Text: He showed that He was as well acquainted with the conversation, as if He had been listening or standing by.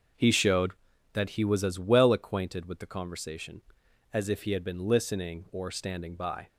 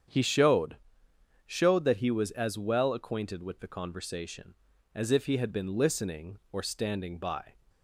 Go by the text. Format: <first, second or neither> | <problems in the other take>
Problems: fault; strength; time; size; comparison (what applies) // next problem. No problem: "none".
first | starts louder than the rest; strong; until 1.7 s; 8.5 dB; also in the first // says "showed" twice; at 1.4 s